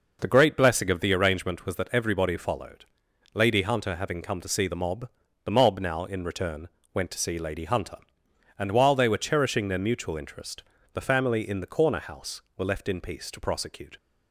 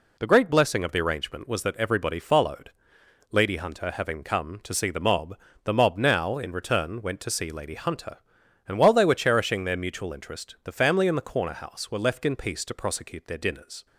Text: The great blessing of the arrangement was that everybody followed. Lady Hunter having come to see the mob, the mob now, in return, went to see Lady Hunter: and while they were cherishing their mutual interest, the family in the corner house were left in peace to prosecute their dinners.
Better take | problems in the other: second | stops before "their dinners"; at 13.9 s

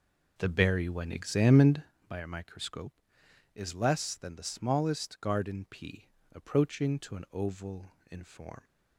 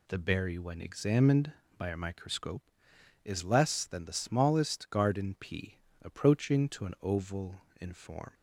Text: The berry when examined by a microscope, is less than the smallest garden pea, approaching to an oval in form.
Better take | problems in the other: second | starts louder than the rest; noticeable; until 1.9 s; 4.5 dB

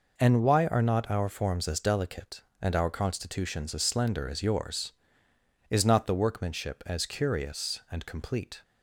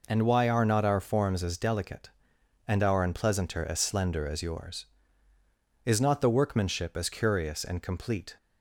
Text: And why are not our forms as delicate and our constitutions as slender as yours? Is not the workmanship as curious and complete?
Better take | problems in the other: first | says "unpleasanter" for "constitutions"; at 3.0 s

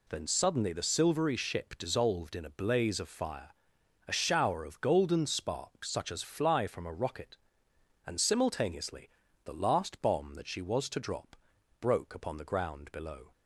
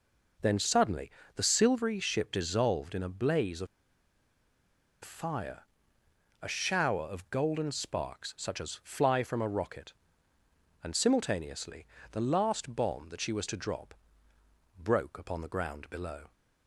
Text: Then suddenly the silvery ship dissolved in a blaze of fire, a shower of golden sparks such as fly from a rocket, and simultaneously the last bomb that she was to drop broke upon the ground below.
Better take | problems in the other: first | pauses between "suddenly" and "the"; slight; at 1.1 s; 0.24 s long // pauses between "of" and "fire"; strong; at 3.6 s; 1.3 s long // pauses between "simultaneously" and "the"; slight; at 11.8 s; 0.26 s long; slight in the first // pauses between "drop" and "broke"; noticeable; at 13.9 s; 0.84 s long; noticeable in the first

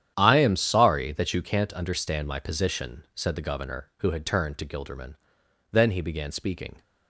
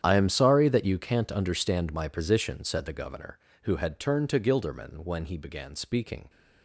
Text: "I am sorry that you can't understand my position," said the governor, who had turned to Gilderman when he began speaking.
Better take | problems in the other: second | starts louder than the rest; strong; until 1.1 s; 10 dB; strong in the second // says "then" for "when"; at 5.7 s

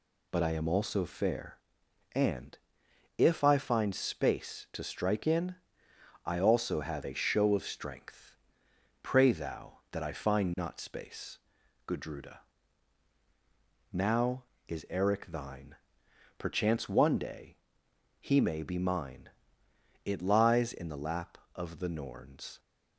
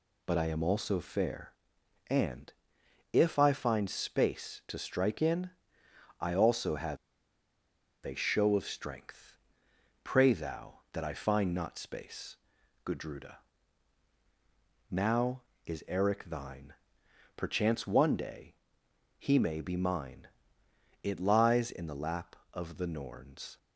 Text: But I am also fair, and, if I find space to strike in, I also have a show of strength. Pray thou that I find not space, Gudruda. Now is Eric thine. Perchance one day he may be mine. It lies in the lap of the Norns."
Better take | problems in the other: first | pauses between "have" and "a"; at 6.9 s; 1.0 s long // pauses between "day" and "he"; noticeable; at 18.5 s; 0.64 s long; noticeable in the first

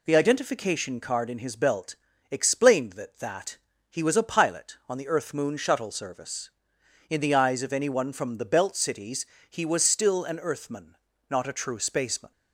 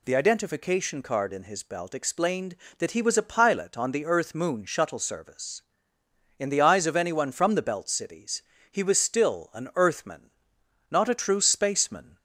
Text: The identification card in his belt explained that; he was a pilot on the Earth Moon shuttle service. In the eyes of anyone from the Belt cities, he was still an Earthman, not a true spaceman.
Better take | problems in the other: second | pauses between "belt" and "explained"; slight; at 1.9 s; 0.34 s long // says "that" twice; at 3.1 s

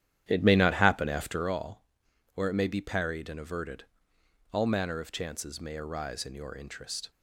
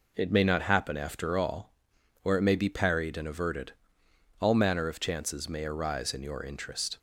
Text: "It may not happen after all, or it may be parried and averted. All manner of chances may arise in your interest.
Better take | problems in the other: second | starts louder than the rest; strong; until 1.6 s; 11 dB

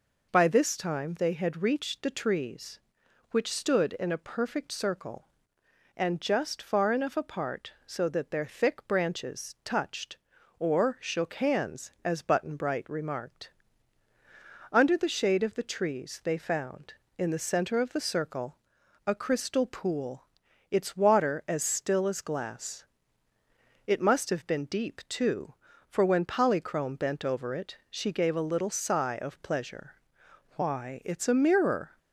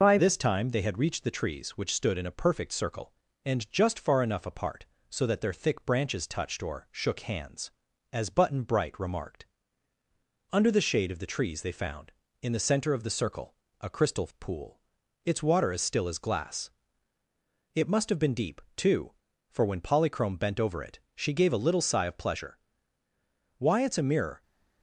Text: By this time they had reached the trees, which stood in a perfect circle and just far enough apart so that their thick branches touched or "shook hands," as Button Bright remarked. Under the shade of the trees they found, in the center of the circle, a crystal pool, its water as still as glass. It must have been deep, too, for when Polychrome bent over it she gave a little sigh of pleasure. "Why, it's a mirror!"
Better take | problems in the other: first | changes voice at "this"; from 0.1 s on; 24.3 s long // pauses between "it" and "she"; slight; at 20.9 s; 0.16 s long

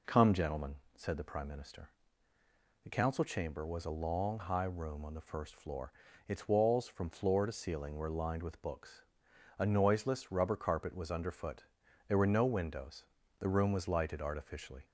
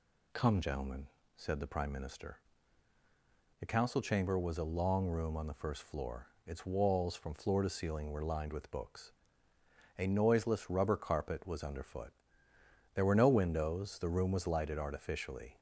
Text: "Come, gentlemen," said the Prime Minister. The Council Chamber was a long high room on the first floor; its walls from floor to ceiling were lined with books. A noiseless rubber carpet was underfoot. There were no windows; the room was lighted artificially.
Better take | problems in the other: first | skips "high"; at 5.0 s

